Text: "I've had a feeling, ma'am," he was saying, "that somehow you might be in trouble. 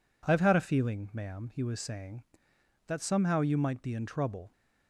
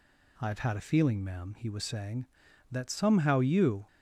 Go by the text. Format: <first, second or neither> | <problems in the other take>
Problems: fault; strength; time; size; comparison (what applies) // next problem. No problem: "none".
first | stops before "might be in trouble"; at 3.8 s